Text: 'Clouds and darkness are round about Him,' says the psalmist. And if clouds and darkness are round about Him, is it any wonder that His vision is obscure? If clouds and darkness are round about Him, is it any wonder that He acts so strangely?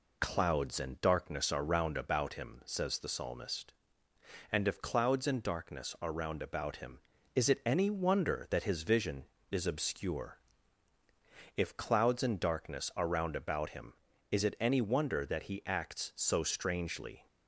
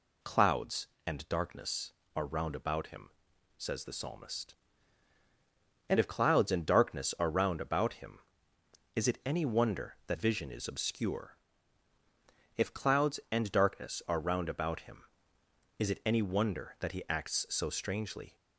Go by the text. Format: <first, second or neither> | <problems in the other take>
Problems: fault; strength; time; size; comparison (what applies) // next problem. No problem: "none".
first | skips "His"; at 10.1 s